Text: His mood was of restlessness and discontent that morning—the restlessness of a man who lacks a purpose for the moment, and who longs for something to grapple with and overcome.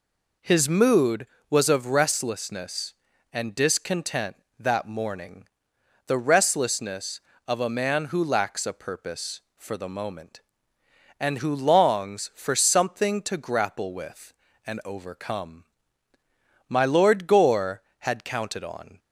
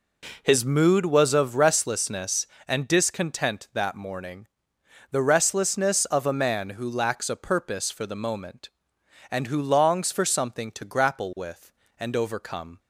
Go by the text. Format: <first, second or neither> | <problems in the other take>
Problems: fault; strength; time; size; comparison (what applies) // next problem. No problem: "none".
second | goes on to say "My Lord Gore had counted on"; strong; from 16.6 s on; 2.3 s long